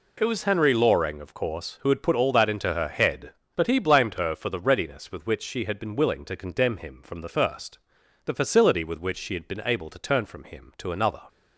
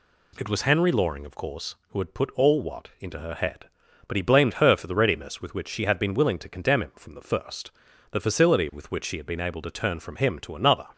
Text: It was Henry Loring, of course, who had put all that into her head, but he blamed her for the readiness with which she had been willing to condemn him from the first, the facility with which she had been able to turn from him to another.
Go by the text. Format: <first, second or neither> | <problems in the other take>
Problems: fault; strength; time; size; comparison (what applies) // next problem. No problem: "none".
first | says "what" for "that"; at 2.5 s